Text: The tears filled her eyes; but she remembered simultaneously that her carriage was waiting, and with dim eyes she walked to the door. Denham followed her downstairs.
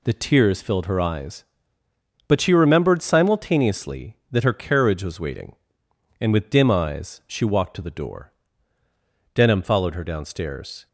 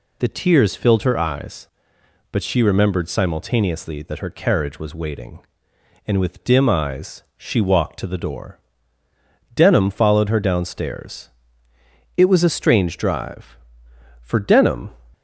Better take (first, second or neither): first